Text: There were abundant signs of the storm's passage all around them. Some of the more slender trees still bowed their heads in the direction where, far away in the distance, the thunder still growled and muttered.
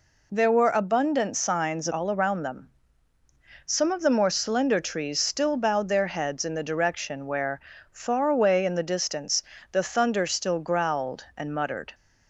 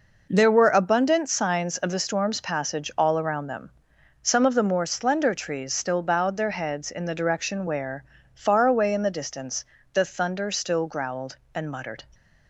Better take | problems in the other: second | skips "of the storm's passage"; at 1.8 s

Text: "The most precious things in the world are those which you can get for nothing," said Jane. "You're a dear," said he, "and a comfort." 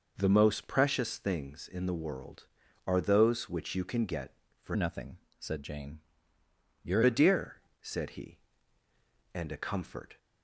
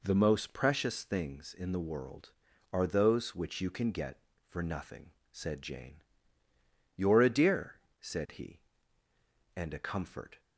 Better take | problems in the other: second | changes voice from "nothing" to "You're"; from 4.7 to 7.0 s; 2.3 s long

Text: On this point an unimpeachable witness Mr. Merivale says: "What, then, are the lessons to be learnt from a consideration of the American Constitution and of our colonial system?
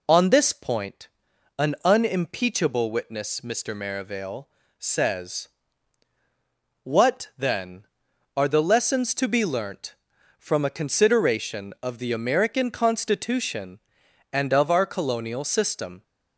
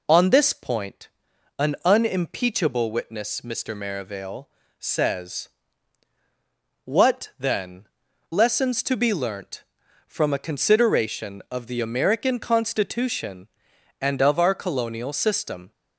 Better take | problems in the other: first | pauses between "point" and "an"; noticeable; at 1.0 s; 0.50 s long; noticeable in the first // pauses between "Merivale" and "says"; slight; at 4.4 s; 0.30 s long; slight in the first // skips "are the"; at 8.0 s

